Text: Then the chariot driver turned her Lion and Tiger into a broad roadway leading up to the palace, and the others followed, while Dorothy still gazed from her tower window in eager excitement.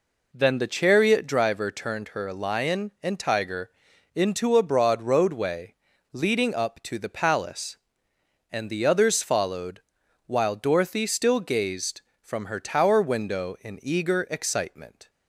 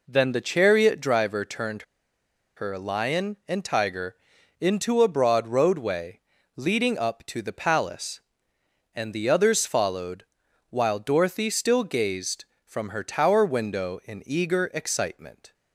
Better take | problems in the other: first | pauses between "turned" and "her"; noticeable; at 1.8 s; 0.73 s long // pauses between "Tiger" and "into"; at 4.1 s; 0.44 s long; also in the first // pauses between "roadway" and "leading"; slight; at 6.2 s; 0.34 s long; slight in the first

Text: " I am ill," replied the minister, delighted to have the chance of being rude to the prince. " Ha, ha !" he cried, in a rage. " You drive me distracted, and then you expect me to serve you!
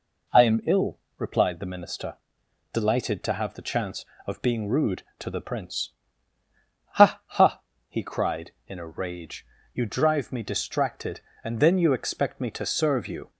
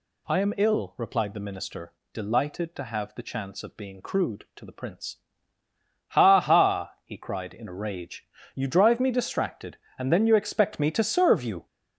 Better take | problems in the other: first | says "crude" for "rude"; at 4.0 s

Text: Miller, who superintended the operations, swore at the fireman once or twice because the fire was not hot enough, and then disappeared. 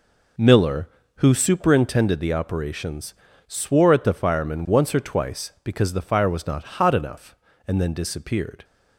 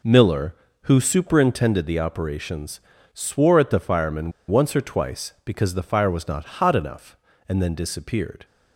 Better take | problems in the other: first | pauses between "fireman" and "once"; slight; at 4.3 s; 0.17 s long

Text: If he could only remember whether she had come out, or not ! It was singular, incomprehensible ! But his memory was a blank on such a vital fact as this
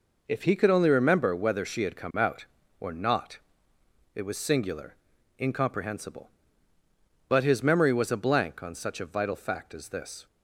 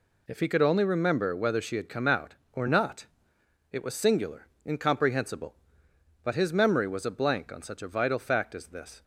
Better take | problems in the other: neither | none

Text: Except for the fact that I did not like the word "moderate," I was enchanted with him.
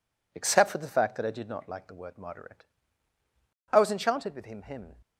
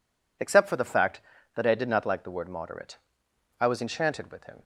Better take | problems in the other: second | says "him" twice; at 4.6 s

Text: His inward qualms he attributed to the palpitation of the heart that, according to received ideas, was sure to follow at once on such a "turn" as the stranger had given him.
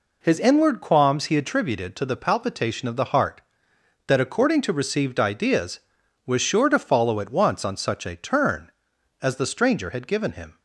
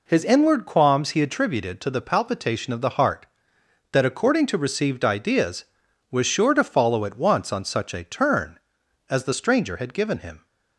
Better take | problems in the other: neither | none

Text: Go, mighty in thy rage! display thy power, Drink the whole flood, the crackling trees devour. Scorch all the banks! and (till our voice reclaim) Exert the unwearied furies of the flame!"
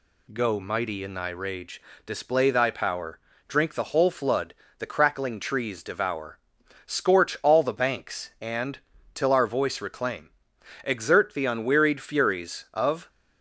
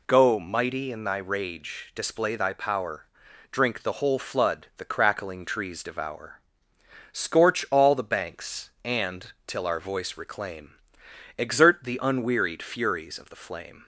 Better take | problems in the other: second | stops before "the flame"; at 13.0 s

